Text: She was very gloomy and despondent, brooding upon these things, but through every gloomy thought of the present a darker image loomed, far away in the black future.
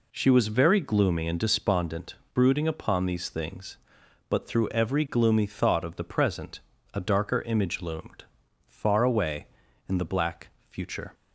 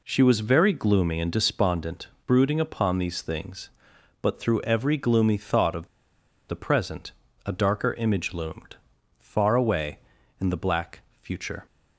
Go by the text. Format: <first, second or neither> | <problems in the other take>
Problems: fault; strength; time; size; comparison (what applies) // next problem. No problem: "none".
first | pauses between "of" and "the"; noticeable; at 5.8 s; 0.62 s long // pauses between "present" and "a"; slight; at 7.1 s; 0.34 s long; slight in the first // pauses between "black" and "future"; slight; at 11.0 s; 0.20 s long; slight in the first